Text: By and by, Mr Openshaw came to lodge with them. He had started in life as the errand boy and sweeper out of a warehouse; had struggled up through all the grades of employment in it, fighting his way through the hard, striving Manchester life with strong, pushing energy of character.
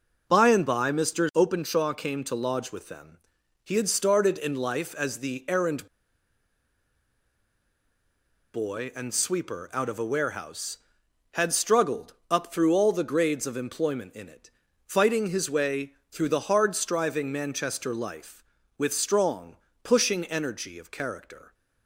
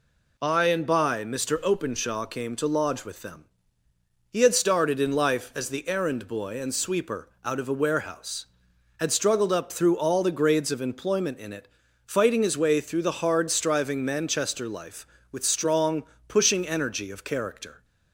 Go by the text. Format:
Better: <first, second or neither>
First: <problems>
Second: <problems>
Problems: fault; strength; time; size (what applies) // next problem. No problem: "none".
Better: second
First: pauses between "errand" and "boy"; strong; at 5.8 s; 2.6 s long // pauses between "struggled" and "up"; slight; at 12.1 s; 0.16 s long // pauses between "way" and "through"; slight; at 15.9 s; 0.18 s long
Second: none